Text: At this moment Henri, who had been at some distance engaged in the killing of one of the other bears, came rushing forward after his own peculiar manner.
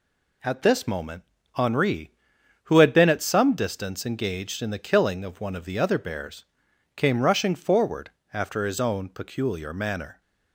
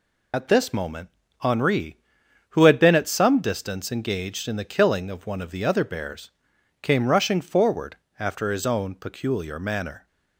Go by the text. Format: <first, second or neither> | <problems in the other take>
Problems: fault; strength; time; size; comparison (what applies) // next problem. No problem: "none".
first | loses the start of "At"; at 0.3 s; 60 ms // pauses between "moment" and "Henri"; slight; at 1.0 s; 0.30 s long; slight in the first // pauses between "forward" and "after"; slight; at 7.9 s; 0.22 s long; slight in the first